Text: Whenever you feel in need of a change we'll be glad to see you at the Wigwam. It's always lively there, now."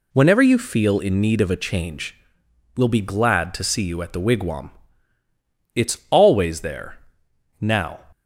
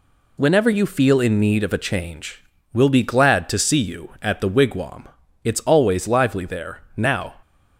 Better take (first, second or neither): second